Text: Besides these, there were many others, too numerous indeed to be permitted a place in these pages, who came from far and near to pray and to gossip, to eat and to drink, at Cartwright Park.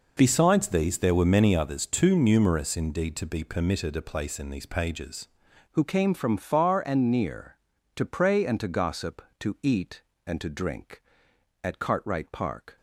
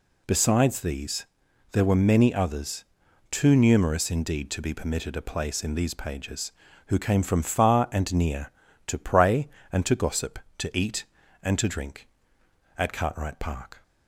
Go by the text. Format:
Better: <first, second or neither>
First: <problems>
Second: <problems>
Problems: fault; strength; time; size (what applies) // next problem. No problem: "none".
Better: second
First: changes voice at "who"; from 5.7 s on; 7.0 s long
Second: none